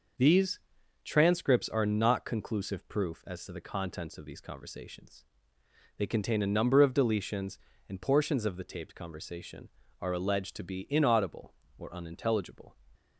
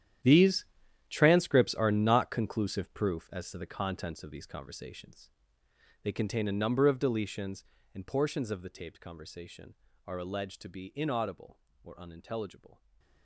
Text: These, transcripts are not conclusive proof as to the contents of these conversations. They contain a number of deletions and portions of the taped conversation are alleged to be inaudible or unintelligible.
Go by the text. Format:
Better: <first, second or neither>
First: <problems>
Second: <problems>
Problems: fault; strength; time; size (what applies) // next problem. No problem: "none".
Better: first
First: starts louder than the rest; noticeable; until 1.6 s; 6 dB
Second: gets quieter; strong; throughout; 15 dB // starts louder than the rest; strong; until 1.6 s; 10.5 dB // stays silent after the last word; slight; from 12.7 s on; 0.5 s long